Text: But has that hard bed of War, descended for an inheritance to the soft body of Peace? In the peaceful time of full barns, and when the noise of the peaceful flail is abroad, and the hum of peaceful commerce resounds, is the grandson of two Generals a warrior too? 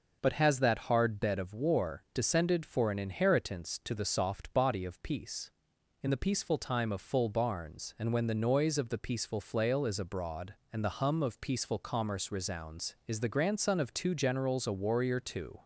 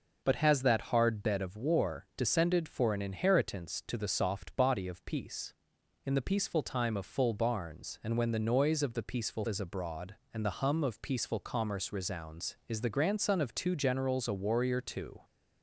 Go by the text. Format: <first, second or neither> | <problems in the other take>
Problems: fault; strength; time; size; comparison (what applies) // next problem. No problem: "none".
first | skips "flail"; at 9.4 s